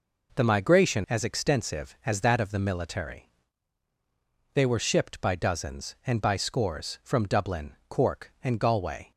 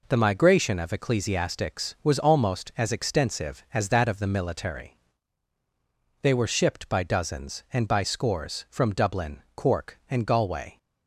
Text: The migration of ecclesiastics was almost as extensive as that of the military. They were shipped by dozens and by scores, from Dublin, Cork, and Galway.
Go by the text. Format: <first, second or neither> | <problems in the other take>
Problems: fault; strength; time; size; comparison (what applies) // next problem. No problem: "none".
second | skips "of ecclesiastics was almost"; at 1.0 s